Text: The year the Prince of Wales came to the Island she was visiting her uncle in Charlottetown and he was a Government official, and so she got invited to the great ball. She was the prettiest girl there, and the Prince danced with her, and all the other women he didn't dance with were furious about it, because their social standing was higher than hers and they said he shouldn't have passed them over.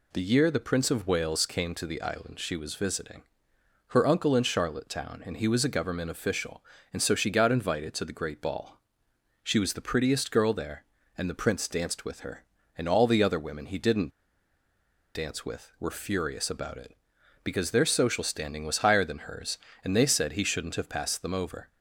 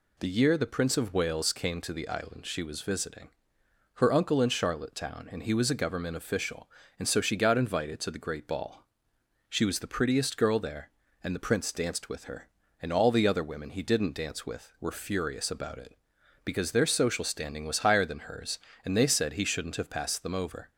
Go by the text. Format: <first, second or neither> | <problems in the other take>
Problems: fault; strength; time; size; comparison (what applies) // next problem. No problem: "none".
second | pauses between "visiting" and "her"; noticeable; at 3.2 s; 0.66 s long; noticeable in the second // pauses between "didn't" and "dance"; at 14.1 s; 1.0 s long